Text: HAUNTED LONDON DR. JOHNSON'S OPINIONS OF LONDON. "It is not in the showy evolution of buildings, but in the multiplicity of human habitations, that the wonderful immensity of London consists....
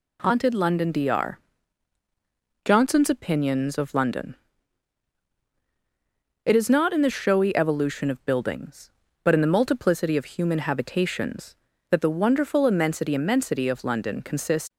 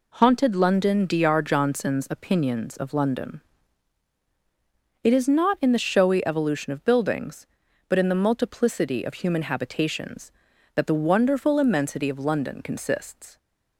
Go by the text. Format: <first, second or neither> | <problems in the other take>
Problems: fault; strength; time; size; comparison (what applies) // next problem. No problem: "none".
second | says "immensity" twice; at 13.1 s